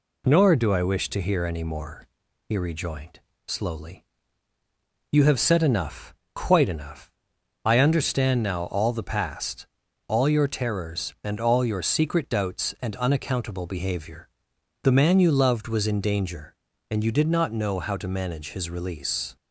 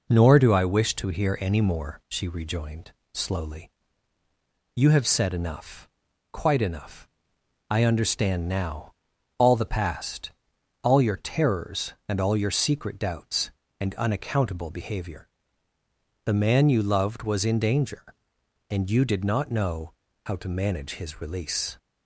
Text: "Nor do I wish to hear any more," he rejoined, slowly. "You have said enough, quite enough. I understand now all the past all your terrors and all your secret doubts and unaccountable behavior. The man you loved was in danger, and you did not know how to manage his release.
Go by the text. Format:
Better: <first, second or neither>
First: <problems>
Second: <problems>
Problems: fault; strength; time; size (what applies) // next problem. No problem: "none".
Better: first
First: pauses between "past" and "all"; at 9.6 s; 0.40 s long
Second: says "she" for "he"; at 2.0 s // pauses between "now" and "all"; at 8.9 s; 0.44 s long // pauses between "past" and "all"; noticeable; at 10.3 s; 0.52 s long // pauses between "know" and "how"; slight; at 19.9 s; 0.34 s long